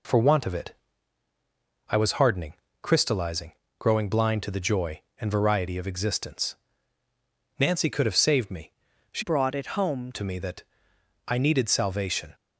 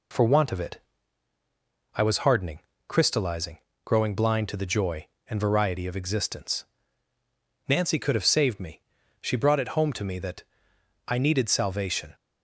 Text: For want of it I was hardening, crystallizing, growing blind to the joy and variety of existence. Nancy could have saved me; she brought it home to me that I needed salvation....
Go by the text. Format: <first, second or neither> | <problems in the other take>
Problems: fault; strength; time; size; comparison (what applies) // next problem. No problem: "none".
second | pauses between "it" and "I"; at 0.7 s; 1.1 s long; also in the second // changes voice from "brought" to "home"; from 9.2 to 10.1 s; 0.9 s long // pauses between "that" and "I"; noticeable; at 10.6 s; 0.62 s long; noticeable in the second